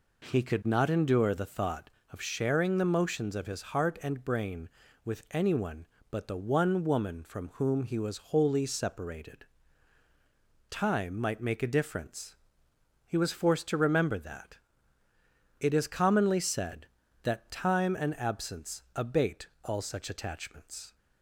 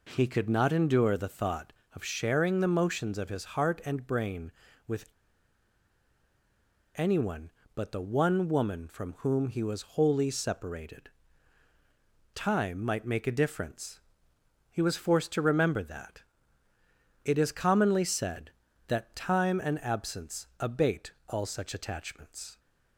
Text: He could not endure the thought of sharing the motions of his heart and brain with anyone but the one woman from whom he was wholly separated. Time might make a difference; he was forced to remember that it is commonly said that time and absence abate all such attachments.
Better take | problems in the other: first | pauses between "with" and "anyone"; strong; at 5.0 s; 1.8 s long // pauses between "that" and "it"; at 16.2 s; 1.0 s long; also in the first // pauses between "abate" and "all"; slight; at 21.1 s; 0.16 s long; slight in the first

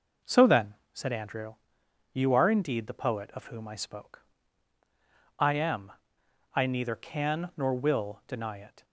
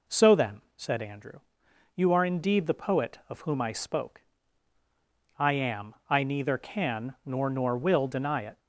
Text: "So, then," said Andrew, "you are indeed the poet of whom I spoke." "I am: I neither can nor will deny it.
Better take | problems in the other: first | says "nor" twice; at 7.4 s

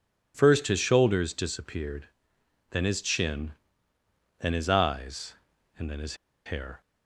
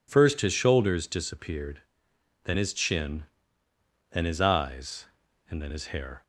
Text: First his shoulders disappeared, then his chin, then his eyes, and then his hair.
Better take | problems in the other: second | pauses between "his" and "hair"; slight; at 6.1 s; 0.30 s long

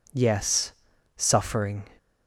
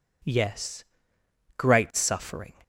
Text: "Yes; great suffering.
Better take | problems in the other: second | skips "great"; at 0.9 s

